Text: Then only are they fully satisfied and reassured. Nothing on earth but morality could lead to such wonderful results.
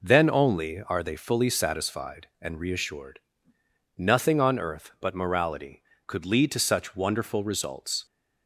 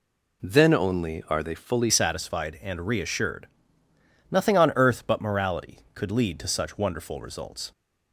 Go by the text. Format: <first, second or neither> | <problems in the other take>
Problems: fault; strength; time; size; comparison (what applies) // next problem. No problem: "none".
first | changes voice at "satisfied"; from 1.8 s on; 5.9 s long